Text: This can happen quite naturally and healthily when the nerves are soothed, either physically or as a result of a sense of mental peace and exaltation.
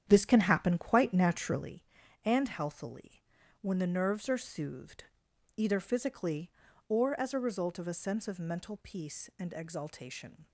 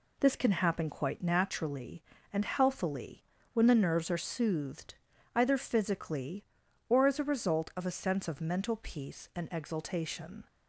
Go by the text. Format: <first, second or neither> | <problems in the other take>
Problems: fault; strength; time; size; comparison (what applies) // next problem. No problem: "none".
second | starts louder than the rest; strong; until 1.7 s; 9 dB // pauses between "healthily" and "when"; at 3.2 s; 0.38 s long; slight in the second